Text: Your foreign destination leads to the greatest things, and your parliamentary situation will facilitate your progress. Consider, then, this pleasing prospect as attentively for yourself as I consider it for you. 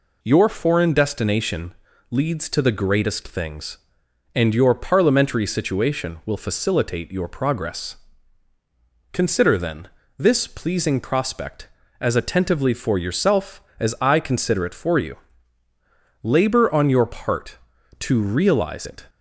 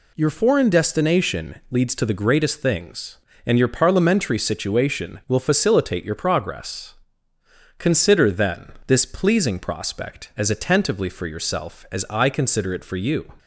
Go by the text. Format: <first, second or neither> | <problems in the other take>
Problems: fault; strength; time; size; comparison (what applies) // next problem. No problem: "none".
second | pauses between "destination" and "leads"; at 1.7 s; 0.38 s long // goes on to say "Labor on your part to realize it"; strong; from 16.2 s on; 2.8 s long